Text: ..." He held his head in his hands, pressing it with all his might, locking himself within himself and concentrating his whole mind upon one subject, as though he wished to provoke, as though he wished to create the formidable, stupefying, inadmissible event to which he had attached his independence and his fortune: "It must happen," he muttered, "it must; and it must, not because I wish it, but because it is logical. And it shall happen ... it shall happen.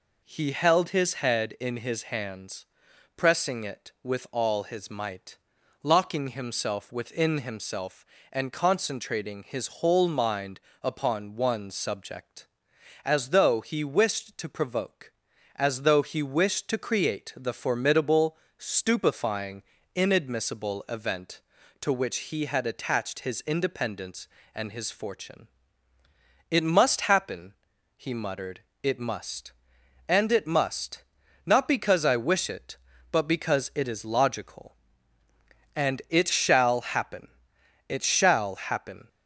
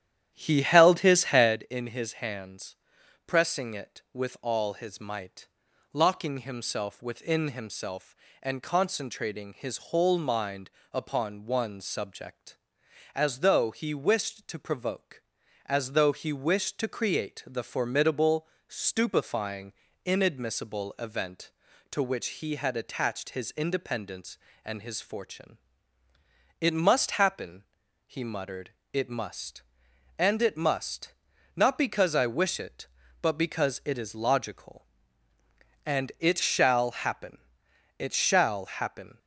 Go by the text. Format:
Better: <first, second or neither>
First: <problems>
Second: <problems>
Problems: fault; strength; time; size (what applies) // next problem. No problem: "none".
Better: first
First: pauses between "mind" and "upon"; slight; at 10.5 s; 0.22 s long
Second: starts louder than the rest; strong; until 1.6 s; 10.5 dB // pauses between "mind" and "upon"; slight; at 10.6 s; 0.22 s long